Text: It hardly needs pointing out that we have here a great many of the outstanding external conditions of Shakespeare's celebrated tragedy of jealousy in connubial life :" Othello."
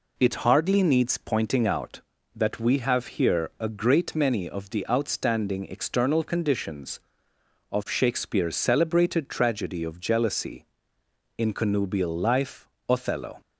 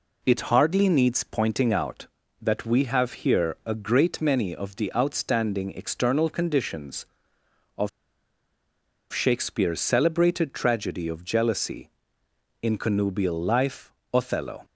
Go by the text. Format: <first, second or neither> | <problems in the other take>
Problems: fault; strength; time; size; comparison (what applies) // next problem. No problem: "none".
first | pauses between "of" and "Shakespeare's"; at 7.8 s; 1.2 s long